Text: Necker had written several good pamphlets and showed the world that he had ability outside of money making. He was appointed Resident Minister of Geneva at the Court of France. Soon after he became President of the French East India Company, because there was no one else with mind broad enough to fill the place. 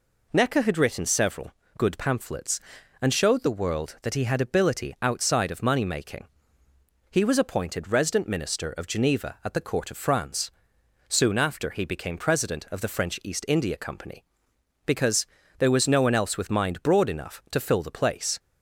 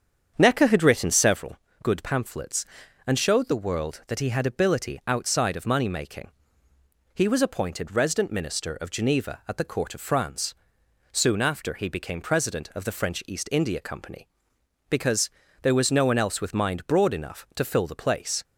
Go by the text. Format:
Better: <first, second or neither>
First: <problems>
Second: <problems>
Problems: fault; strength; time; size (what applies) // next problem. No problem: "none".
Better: first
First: pauses between "several" and "good"; slight; at 1.5 s; 0.26 s long // pauses between "because" and "there"; slight; at 15.2 s; 0.34 s long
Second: starts louder than the rest; strong; until 1.4 s; 8 dB // pauses between "several" and "good"; slight; at 1.5 s; 0.26 s long // pauses between "because" and "there"; slight; at 15.2 s; 0.34 s long